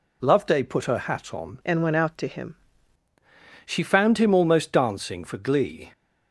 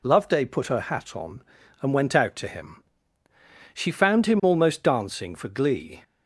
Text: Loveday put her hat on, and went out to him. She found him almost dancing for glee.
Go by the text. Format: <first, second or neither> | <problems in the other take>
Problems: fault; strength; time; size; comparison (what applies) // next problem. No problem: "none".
second | changes voice from "and" to "him"; from 1.6 to 2.5 s; 0.9 s long